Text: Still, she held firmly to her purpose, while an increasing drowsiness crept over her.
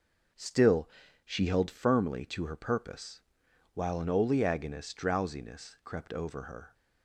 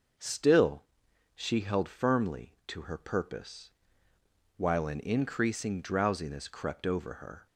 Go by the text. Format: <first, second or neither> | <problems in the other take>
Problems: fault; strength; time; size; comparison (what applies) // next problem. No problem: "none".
second | says "oleaginous" for "increasing"; at 4.0 s